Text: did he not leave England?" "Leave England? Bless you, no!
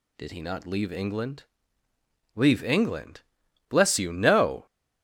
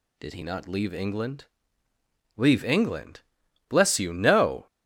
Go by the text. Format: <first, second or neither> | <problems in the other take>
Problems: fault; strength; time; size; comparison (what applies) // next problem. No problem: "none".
neither | none